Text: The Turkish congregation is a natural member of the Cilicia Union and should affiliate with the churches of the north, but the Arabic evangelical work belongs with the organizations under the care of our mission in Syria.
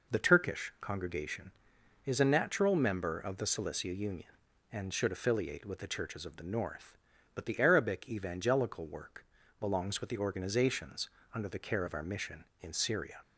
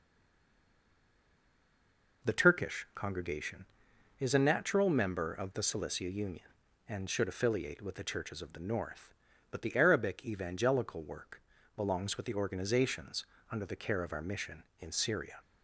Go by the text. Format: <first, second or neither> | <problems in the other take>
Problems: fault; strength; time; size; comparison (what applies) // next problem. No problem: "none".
first | stays silent before the first word; until 2.2 s; 2.2 s long // pauses between "work" and "belongs"; slight; at 11.4 s; 0.34 s long; slight in the first // pauses between "organizations" and "under"; slight; at 13.2 s; 0.24 s long; slight in the first